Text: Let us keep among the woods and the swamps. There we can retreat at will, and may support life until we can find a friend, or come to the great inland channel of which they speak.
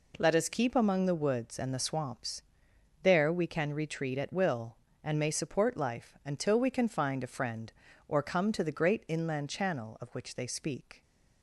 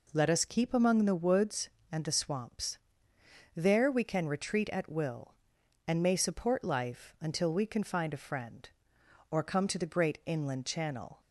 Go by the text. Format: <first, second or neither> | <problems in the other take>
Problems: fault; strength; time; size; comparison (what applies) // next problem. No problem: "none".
first | stops before "of which they speak"; at 11.1 s